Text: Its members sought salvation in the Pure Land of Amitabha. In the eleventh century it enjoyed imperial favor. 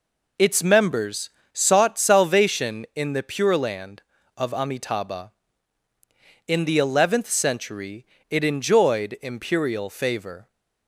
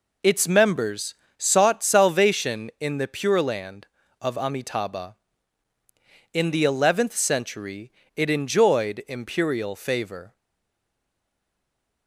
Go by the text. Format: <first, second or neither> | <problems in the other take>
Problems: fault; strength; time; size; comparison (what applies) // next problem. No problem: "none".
first | pauses between "members" and "sought"; slight; at 1.1 s; 0.22 s long; slight in the first // pauses between "century" and "it"; slight; at 7.9 s; 0.24 s long; slight in the first // stays silent after the last word; noticeable; from 10.3 s on; 1.7 s long